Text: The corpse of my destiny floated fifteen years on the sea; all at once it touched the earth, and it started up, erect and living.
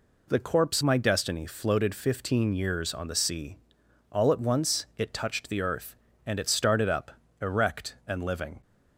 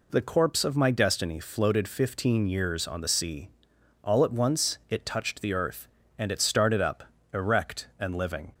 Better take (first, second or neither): second